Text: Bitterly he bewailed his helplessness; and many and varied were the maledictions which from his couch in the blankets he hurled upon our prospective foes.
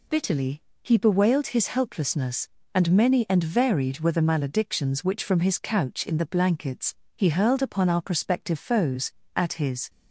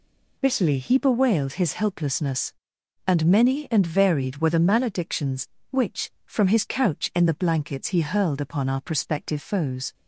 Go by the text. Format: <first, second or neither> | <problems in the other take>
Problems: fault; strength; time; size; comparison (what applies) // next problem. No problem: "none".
second | pauses between "Bitterly" and "he"; slight; at 0.6 s; 0.20 s long // pauses between "blankets" and "he"; slight; at 6.9 s; 0.20 s long // goes on to say "At his"; from 9.3 s on; 0.54 s long